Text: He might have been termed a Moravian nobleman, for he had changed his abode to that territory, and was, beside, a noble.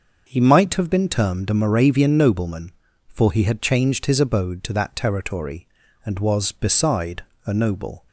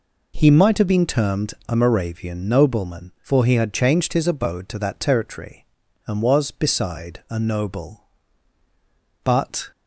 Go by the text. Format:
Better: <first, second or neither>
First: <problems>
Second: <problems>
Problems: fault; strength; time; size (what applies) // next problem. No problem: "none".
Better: first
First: none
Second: pauses between "termed" and "a"; slight; at 1.5 s; 0.16 s long // goes on to say "But"; slight; from 9.2 s on; 0.48 s long